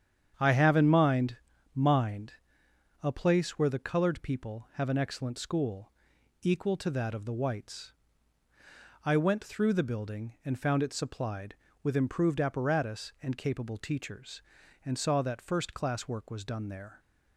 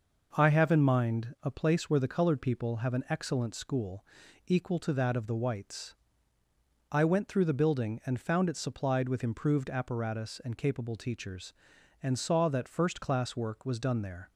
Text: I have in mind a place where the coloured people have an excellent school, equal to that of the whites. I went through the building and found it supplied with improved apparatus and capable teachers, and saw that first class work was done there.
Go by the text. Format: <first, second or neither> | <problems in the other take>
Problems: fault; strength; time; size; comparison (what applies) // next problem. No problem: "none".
second | starts louder than the rest; strong; until 1.3 s; 8.5 dB // says "mind" twice; at 1.7 s